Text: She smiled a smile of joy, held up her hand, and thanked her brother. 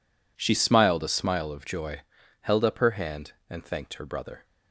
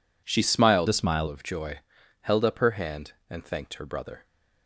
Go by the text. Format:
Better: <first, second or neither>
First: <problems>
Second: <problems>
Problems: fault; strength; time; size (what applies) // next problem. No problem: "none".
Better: first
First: none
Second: changes voice from "a" to "smile"; from 0.8 to 1.2 s; 0.4 s long